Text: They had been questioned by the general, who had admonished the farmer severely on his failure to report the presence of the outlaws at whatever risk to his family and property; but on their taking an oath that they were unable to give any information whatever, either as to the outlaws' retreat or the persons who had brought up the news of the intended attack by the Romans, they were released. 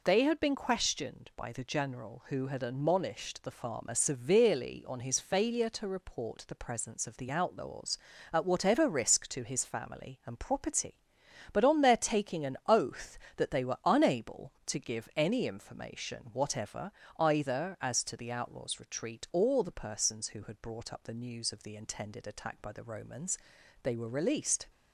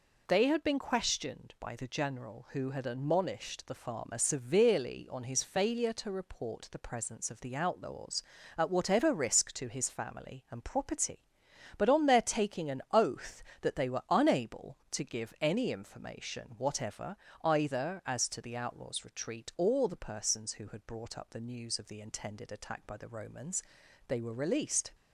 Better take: neither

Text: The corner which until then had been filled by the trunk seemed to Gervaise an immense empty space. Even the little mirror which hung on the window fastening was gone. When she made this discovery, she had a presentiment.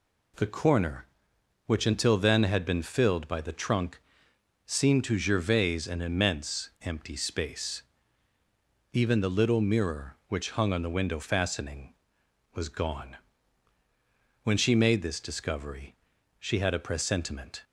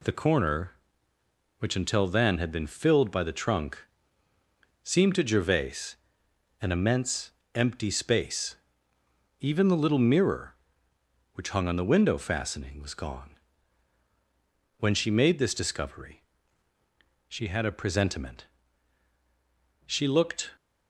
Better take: first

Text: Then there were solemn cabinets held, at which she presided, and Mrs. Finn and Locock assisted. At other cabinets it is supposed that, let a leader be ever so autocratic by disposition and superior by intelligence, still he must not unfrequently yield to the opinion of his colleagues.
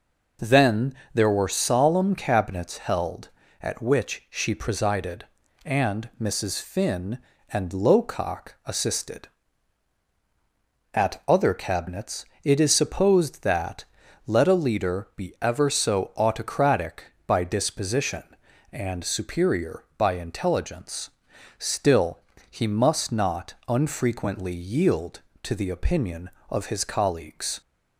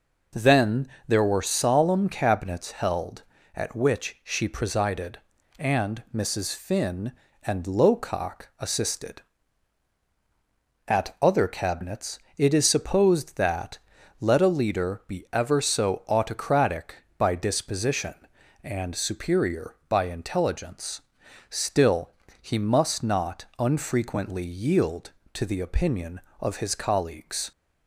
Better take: neither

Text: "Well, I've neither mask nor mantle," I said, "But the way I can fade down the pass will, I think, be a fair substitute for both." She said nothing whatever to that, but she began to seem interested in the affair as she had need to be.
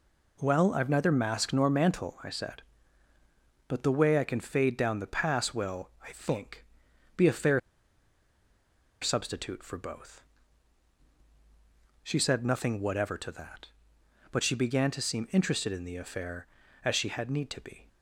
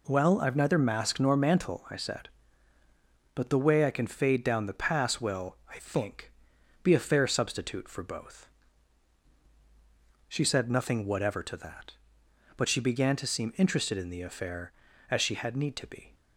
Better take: second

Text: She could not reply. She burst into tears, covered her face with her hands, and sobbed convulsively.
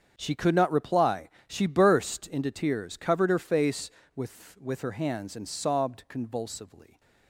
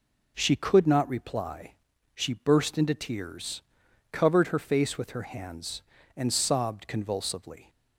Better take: second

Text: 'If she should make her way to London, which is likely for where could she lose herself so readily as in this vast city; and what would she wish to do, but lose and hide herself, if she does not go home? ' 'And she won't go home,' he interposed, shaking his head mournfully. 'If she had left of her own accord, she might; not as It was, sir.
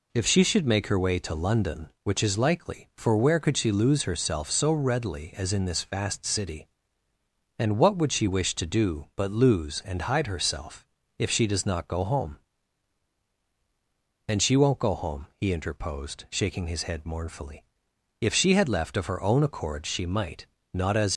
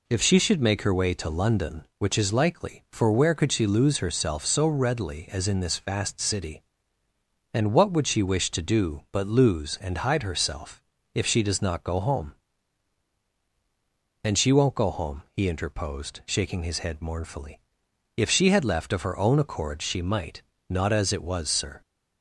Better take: second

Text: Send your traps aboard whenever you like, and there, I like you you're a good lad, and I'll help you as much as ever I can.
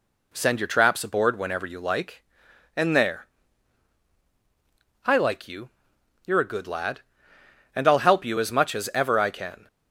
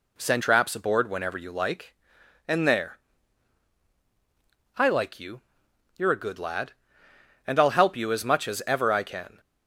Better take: first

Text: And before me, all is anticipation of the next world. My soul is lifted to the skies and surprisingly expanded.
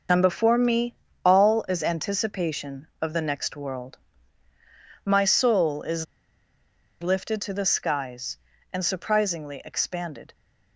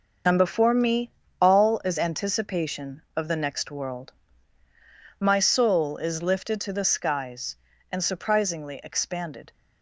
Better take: second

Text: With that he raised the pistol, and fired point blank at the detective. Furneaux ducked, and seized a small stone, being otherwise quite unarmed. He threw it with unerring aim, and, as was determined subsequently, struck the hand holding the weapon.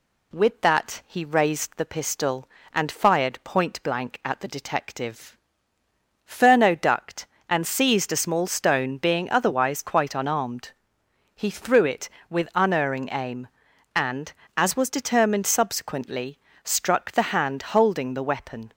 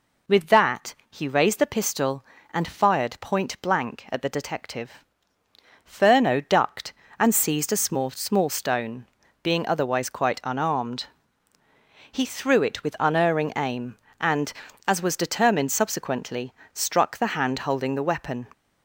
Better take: first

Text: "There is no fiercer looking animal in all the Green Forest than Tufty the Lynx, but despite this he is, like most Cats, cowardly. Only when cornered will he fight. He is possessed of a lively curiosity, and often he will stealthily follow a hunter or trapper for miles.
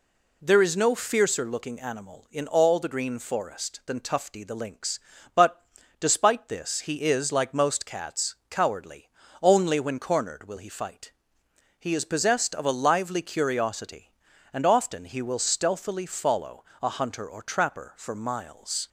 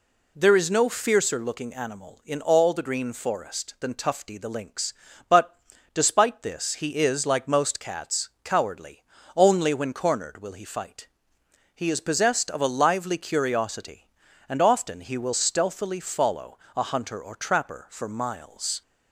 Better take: neither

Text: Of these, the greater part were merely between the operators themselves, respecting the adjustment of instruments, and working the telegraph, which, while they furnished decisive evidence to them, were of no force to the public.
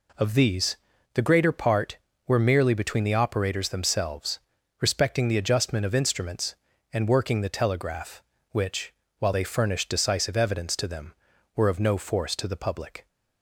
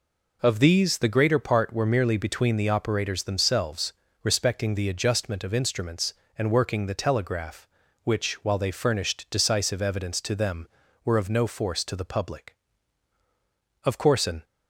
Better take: first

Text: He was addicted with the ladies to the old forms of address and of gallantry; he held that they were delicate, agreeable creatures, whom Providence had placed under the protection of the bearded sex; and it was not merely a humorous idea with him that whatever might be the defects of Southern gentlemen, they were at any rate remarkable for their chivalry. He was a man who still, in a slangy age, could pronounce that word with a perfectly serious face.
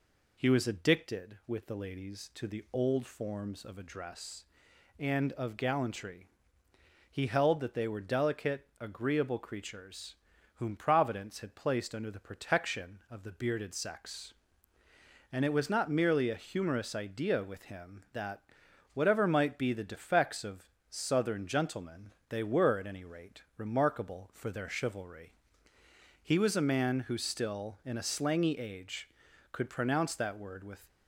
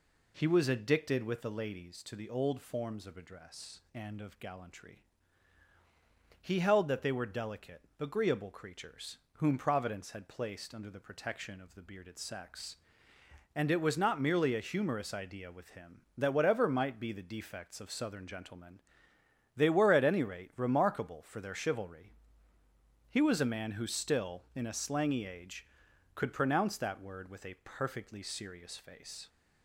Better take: second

